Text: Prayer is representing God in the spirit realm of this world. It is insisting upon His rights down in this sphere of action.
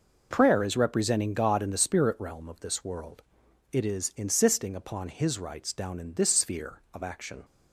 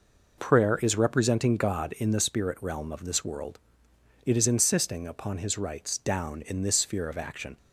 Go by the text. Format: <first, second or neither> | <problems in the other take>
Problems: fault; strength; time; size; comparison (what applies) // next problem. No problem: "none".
neither | none